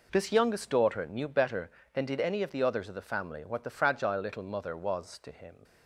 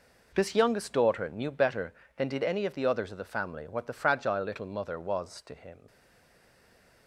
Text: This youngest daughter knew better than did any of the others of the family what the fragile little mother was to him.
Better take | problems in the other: first | stays silent after the last word; noticeable; from 5.8 s on; 1.2 s long

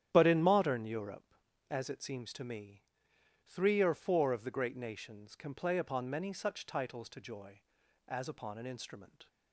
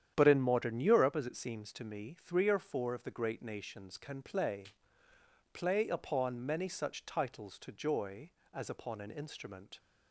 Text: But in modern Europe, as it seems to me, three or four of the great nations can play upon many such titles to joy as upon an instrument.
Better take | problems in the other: first | starts louder than the rest; strong; until 1.1 s; 9.5 dB; strong in the first // says "play" twice; at 5.5 s

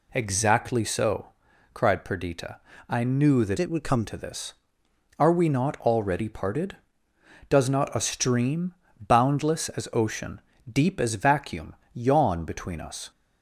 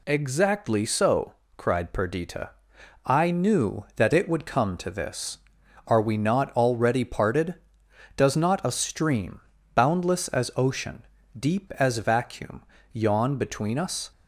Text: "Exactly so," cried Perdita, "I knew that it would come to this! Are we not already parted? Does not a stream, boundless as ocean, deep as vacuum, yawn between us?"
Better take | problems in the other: second | changes voice from "it" to "come"; from 3.5 to 4.0 s; 0.5 s long

